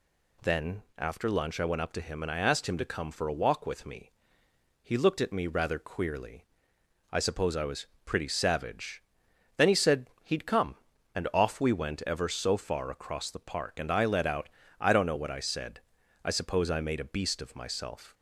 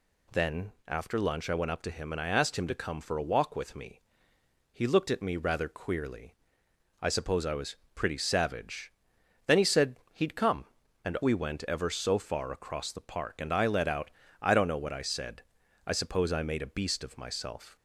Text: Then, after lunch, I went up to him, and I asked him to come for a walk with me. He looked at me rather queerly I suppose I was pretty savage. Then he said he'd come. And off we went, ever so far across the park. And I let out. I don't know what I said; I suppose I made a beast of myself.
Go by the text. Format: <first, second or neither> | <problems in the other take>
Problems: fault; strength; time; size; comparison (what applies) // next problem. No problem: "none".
first | pauses between "queerly" and "I"; noticeable; at 6.3 s; 0.66 s long; noticeable in the first // pauses between "was" and "pretty"; slight; at 7.7 s; 0.18 s long; slight in the first // pauses between "said" and "he'd"; slight; at 9.9 s; 0.16 s long; slight in the first // skips "off"; at 11.1 s